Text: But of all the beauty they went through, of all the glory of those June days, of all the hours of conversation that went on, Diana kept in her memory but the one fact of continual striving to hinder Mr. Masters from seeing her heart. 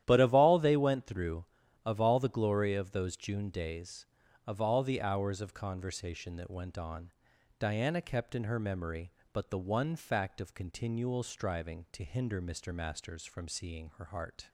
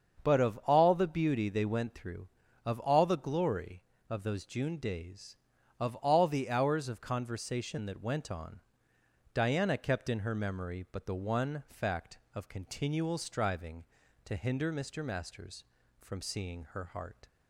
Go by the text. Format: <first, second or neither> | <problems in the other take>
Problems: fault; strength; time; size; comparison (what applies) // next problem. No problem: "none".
second | starts louder than the rest; strong; until 1.0 s; 12 dB; strong in the second // skips "the beauty"; at 0.5 s